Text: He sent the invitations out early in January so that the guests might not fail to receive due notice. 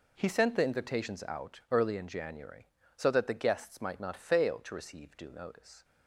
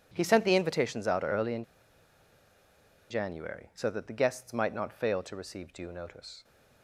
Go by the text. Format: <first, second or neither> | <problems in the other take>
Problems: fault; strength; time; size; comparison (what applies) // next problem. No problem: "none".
first | pauses between "in" and "January"; strong; at 1.6 s; 1.4 s long